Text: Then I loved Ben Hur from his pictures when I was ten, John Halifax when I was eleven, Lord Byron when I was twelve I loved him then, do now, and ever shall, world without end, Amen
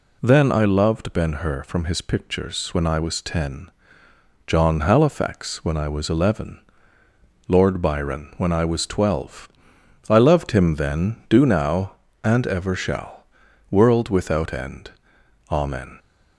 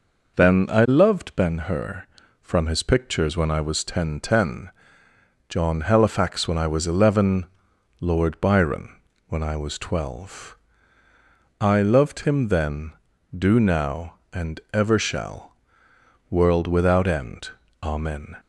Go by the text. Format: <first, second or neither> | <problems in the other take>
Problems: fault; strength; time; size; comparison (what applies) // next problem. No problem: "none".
first | says "ten" twice; at 4.1 s // pauses between "Byron" and "when"; slight; at 8.9 s; 0.32 s long // pauses between "twelve" and "I"; at 10.5 s; 1.0 s long; noticeable in the first